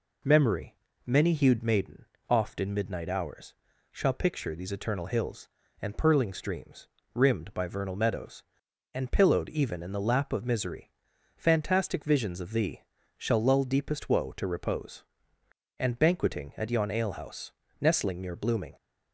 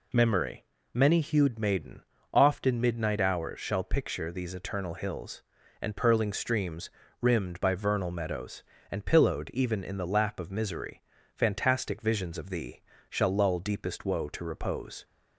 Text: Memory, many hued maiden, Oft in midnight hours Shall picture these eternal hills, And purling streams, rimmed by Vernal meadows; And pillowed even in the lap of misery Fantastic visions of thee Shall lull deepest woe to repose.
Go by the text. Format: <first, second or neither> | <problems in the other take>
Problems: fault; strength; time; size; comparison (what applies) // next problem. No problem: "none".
second | pauses between "hours" and "Shall"; slight; at 3.5 s; 0.36 s long // pauses between "misery" and "Fantastic"; noticeable; at 10.9 s; 0.46 s long; slight in the second // pauses between "thee" and "Shall"; slight; at 12.8 s; 0.34 s long; slight in the second // goes on to say "And banqueting at yon alehouse Nestling near blooming"; strong; from 15.7 s on; 2.9 s long